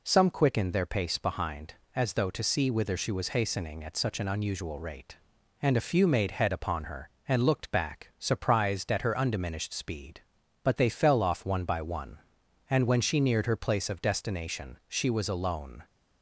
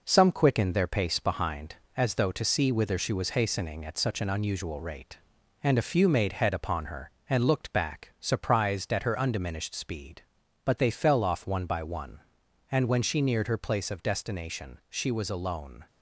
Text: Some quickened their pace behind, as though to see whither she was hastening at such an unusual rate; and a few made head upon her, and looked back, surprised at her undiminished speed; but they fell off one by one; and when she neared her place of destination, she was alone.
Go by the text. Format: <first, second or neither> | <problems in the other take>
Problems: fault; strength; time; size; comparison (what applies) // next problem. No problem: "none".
first | gets quieter; noticeable; throughout; 4.5 dB